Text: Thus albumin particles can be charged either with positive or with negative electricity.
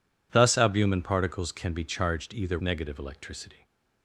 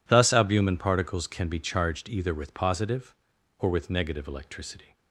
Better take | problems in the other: second | skips "with positive or with"; at 2.5 s

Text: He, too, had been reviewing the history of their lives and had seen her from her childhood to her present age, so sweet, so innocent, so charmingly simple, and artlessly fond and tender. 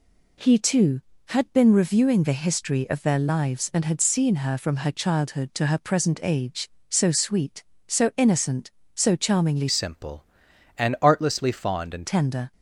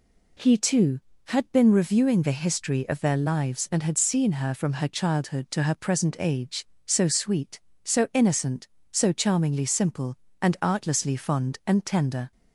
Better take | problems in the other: second | changes voice from "simple" to "and"; from 9.6 to 12.0 s; 2.4 s long

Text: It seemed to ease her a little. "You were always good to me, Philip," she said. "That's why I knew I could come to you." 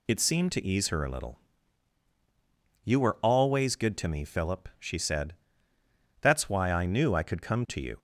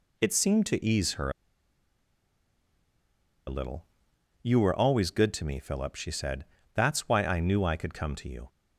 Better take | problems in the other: first | pauses between "her" and "a"; strong; at 1.2 s; 2.1 s long

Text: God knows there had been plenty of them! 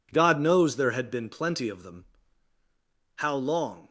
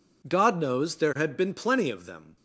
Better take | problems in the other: second | goes on to say "How long"; noticeable; from 3.1 s on; 0.72 s long

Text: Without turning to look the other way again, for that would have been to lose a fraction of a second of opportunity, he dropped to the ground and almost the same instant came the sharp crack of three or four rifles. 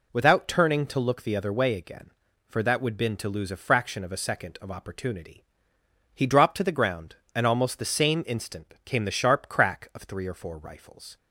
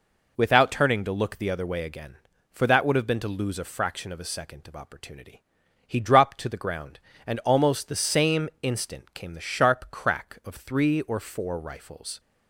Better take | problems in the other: second | skips "have"; at 2.9 s

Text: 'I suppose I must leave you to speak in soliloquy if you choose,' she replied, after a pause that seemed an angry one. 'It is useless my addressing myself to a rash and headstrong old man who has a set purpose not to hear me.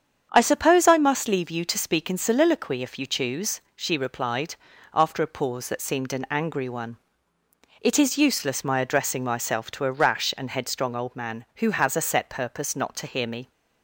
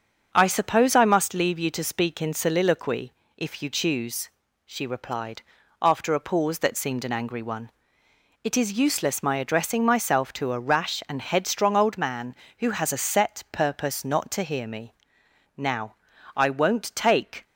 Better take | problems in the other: first | starts louder than the rest; until 1.3 s; 7 dB; strong in the first // pauses between "soliloquy" and "if"; slight; at 3.1 s; 0.24 s long // goes on to say "Now I won't take"; strong; from 15.5 s on; 1.8 s long

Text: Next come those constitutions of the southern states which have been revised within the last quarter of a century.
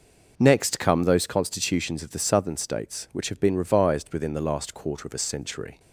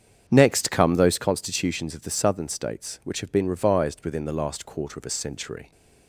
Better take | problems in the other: first | starts louder than the rest; strong; until 1.5 s; 7.5 dB

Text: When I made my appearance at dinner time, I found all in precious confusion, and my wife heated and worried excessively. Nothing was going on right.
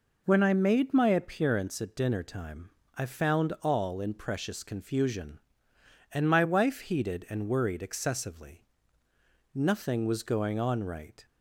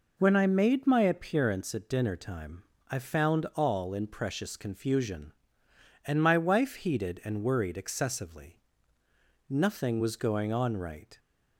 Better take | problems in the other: neither | none

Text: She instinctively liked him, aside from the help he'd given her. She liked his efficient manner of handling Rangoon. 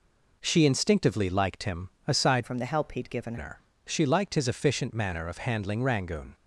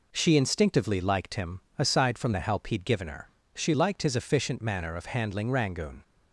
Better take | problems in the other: second | changes voice from "from" to "given"; from 2.4 to 3.3 s; 0.9 s long

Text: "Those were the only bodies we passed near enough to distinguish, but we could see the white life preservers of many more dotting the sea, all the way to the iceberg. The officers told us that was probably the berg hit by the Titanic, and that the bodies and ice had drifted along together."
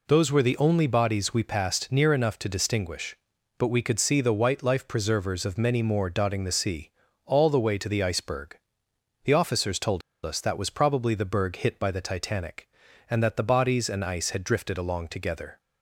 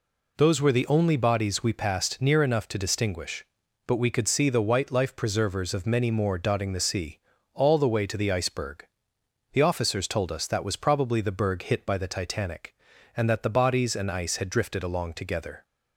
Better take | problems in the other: second | pauses between "told" and "us"; slight; at 10.0 s; 0.24 s long

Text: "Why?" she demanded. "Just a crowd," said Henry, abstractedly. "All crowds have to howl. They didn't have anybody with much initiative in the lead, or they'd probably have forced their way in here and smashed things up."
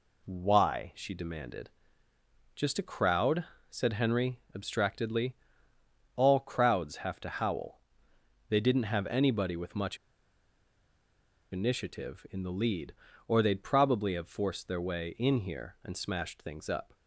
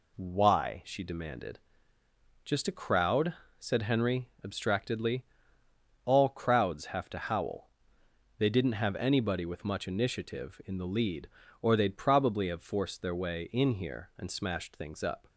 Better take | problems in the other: second | pauses between "much" and "initiative"; strong; at 9.9 s; 1.5 s long

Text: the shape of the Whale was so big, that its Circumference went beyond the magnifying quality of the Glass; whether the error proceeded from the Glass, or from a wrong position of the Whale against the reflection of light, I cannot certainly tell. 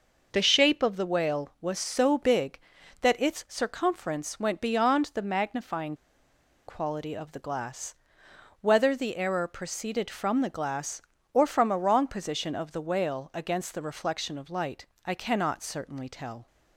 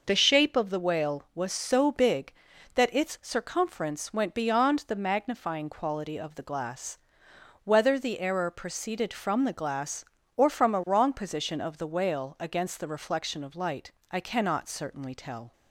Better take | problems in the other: second | pauses between "magnifying" and "quality"; noticeable; at 5.9 s; 0.73 s long

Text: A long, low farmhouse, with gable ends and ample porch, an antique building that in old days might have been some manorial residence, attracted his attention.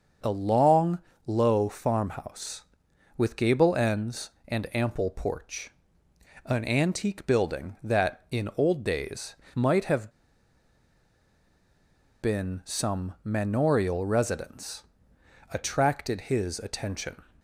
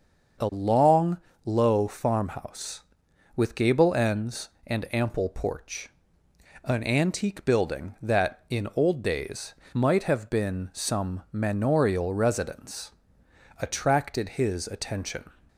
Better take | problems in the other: second | starts louder than the rest; until 1.5 s; 6.5 dB; also in the second // pauses between "days" and "might"; slight; at 9.3 s; 0.18 s long; slight in the second // pauses between "have" and "been"; strong; at 10.0 s; 2.1 s long

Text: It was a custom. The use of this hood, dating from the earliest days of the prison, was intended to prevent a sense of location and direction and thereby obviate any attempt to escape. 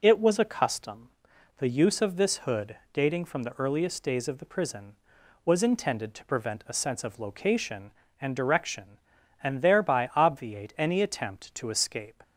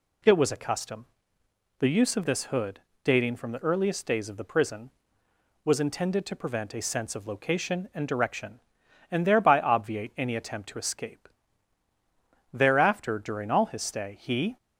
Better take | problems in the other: first | goes on to say "Thereafter during all his stay he"; strong; from 12.5 s on; 2.0 s long

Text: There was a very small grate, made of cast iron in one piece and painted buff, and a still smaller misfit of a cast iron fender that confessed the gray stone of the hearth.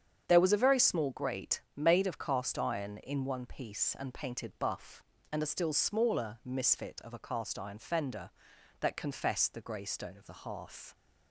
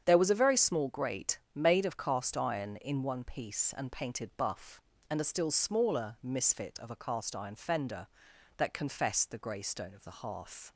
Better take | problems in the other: neither | starts louder than the rest; strong; the same in both

